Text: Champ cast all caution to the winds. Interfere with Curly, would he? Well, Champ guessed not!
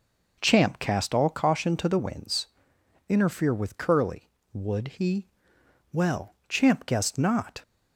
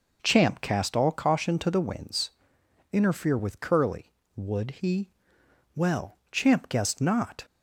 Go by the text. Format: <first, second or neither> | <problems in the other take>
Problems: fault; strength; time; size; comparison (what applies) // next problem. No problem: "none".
neither | none